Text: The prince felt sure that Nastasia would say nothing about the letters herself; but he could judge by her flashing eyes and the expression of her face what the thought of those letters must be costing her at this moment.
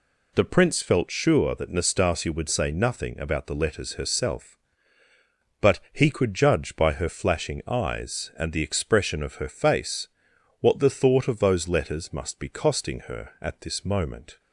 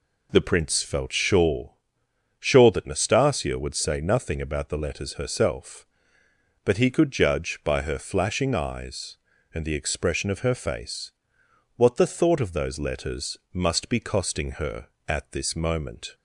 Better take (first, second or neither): first